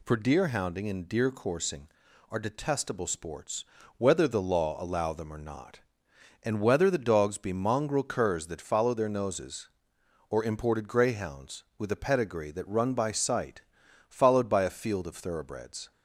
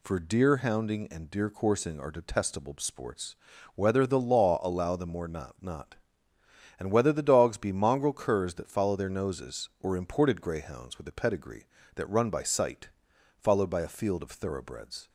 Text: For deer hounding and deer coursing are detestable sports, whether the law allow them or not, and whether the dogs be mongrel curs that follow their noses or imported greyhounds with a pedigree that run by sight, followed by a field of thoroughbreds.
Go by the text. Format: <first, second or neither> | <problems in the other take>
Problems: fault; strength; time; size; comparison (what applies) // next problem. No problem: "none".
first | says "not" twice; at 5.6 s